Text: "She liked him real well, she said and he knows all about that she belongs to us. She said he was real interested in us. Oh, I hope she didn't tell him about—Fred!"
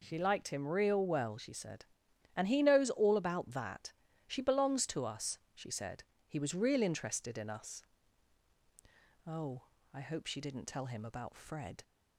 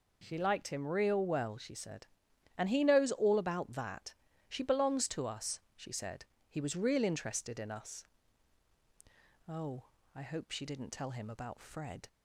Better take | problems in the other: neither | pauses between "that" and "she"; slight; the same in both // pauses between "said" and "he"; slight; the same in both

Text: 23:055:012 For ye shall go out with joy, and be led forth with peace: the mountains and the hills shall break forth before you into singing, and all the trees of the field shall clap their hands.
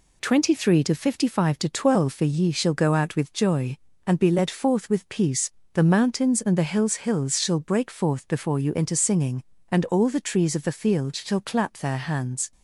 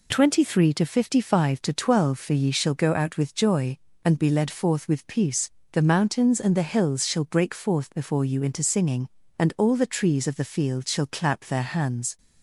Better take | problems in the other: second | says "hills" twice; at 6.9 s

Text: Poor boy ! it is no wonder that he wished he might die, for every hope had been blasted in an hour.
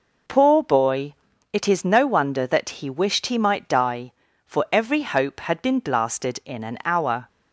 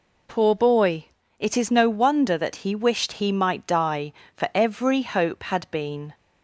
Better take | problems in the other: first | stops before "blasted in an hour"; at 6.1 s

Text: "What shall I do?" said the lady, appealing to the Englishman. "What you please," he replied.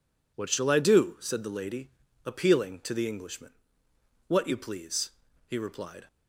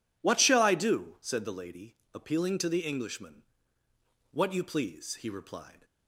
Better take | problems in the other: neither | none

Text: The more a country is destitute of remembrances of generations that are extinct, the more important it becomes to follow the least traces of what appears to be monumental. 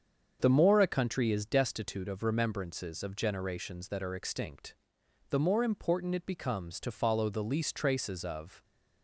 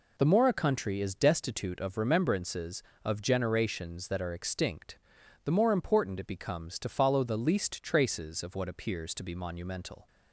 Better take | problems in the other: second | starts louder than the rest; until 1.4 s; 7 dB // stops before "what appears to be monumental"; at 8.6 s

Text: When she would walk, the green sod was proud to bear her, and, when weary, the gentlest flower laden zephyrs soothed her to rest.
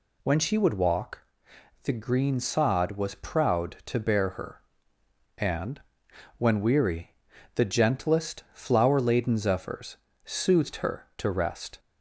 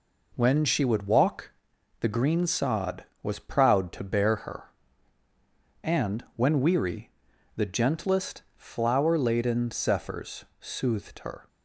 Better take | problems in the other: first | pauses between "gentlest" and "flower"; slight; at 8.4 s; 0.16 s long // pauses between "zephyrs" and "soothed"; slight; at 10.4 s; 0.16 s long; slight in the first // stops before "to rest"; at 11.4 s

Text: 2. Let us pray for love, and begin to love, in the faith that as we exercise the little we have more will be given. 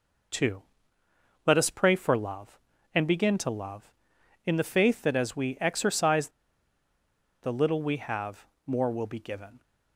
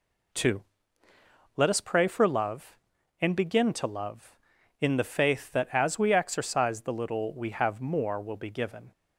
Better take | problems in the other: second | pauses between "exercise" and "the"; at 6.2 s; 1.1 s long // pauses between "have" and "more"; slight; at 8.4 s; 0.20 s long

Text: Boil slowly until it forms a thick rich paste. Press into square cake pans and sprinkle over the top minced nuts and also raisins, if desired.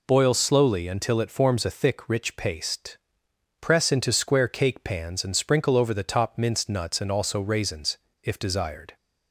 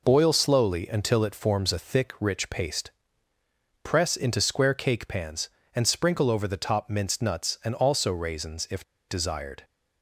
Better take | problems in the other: first | pauses between "if" and "desired"; slight; at 8.8 s; 0.24 s long

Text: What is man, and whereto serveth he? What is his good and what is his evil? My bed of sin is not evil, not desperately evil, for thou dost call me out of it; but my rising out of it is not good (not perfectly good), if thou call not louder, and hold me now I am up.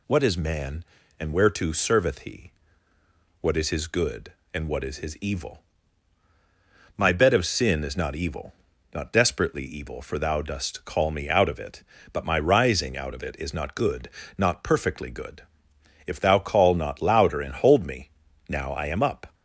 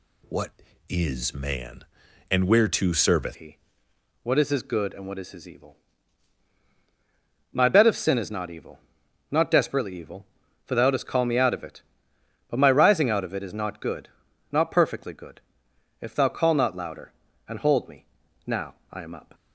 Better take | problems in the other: first | changes voice at "he"; from 3.3 s on; 16.0 s long // pauses between "me" and "now"; at 18.0 s; 0.42 s long; also in the first // pauses between "now" and "I"; slight; at 18.7 s; 0.18 s long

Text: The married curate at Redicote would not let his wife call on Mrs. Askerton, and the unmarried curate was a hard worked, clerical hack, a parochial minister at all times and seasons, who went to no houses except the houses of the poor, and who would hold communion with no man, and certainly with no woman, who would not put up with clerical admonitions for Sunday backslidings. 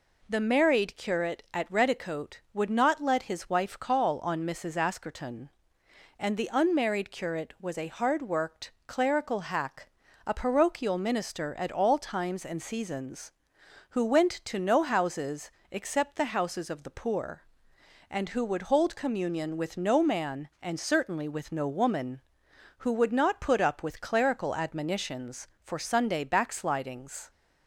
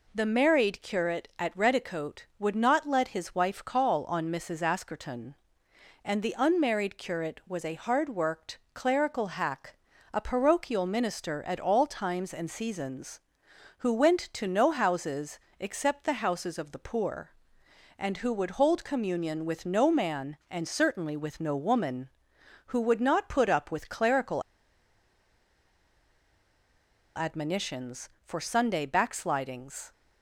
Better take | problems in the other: first | pauses between "houses" and "except"; slight; at 15.3 s; 0.20 s long; slight in the first // pauses between "clerical" and "admonitions"; strong; at 24.4 s; 2.7 s long

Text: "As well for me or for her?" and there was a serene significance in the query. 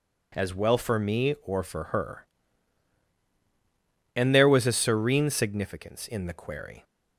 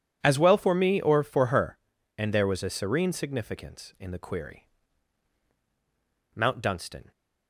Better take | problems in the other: first | goes on to say "Mount Dunstan"; noticeable; from 6.3 s on; 0.76 s long

